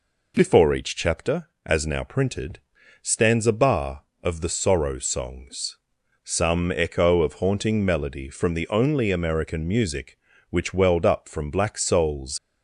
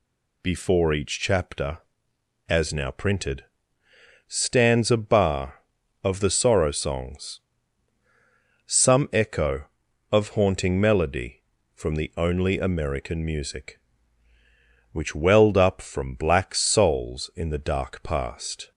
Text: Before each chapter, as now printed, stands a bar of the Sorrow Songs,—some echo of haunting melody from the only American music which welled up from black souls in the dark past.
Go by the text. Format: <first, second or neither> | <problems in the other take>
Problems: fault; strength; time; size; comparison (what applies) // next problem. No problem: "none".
second | stops before "in the dark past"; at 12.3 s